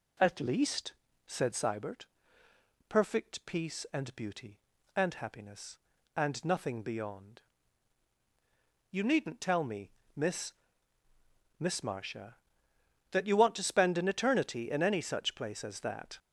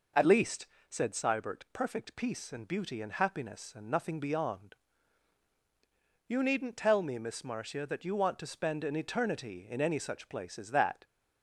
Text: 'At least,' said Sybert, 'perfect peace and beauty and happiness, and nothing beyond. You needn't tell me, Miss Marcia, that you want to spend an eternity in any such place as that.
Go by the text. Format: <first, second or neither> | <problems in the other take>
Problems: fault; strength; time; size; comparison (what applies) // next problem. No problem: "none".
second | says "Miss" twice; at 11.6 s